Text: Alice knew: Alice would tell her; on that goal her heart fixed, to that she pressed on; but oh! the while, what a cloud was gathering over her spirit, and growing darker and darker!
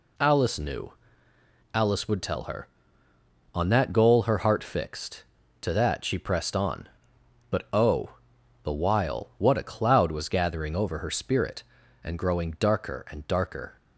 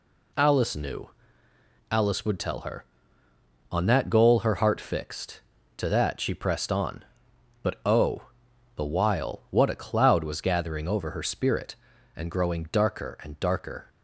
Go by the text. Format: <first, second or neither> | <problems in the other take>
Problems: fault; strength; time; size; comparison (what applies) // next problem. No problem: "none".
neither | none